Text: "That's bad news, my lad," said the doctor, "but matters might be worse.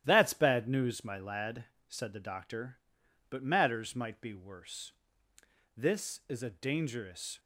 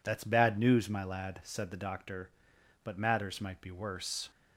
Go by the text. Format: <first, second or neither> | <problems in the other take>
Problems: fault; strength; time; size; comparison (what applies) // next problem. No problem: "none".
second | starts louder than the rest; strong; until 1.0 s; 12 dB // goes on to say "This is a dangerous"; from 5.7 s on; 1.6 s long